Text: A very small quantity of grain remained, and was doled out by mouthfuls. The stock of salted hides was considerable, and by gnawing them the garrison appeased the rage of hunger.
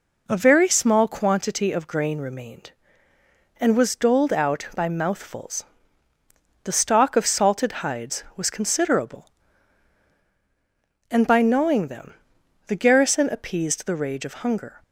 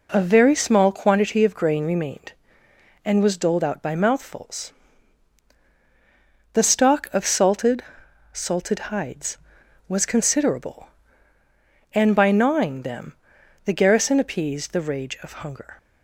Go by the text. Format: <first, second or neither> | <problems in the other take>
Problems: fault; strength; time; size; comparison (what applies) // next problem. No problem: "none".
first | says "salted" twice; at 8.3 s // pauses between "them" and "the"; noticeable; at 13.1 s; 0.54 s long; noticeable in the first